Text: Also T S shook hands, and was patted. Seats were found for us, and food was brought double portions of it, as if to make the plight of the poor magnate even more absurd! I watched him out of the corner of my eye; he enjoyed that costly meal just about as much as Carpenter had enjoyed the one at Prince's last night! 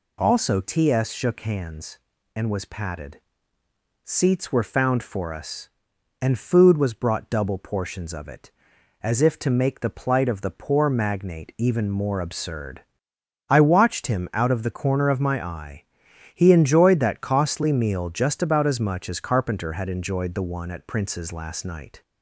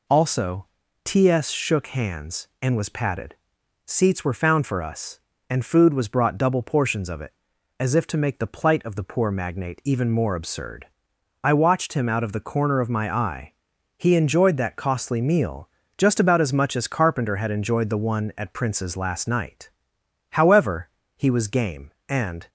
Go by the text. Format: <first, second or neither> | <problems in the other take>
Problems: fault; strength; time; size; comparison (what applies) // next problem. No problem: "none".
first | pauses between "Also" and "T"; slight; at 0.6 s; 0.36 s long // pauses between "meal" and "just"; slight; at 15.6 s; 0.26 s long // goes on to say "However he was game and"; strong; from 20.3 s on; 2.1 s long